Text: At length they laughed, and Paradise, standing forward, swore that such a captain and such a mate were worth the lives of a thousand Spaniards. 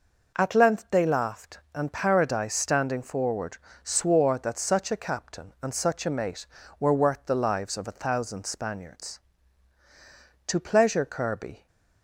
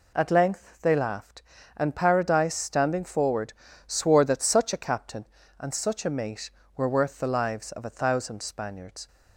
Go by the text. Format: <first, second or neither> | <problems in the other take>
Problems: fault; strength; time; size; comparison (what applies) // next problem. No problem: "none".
second | goes on to say "To pleasure Kirby"; noticeable; from 10.4 s on; 1.2 s long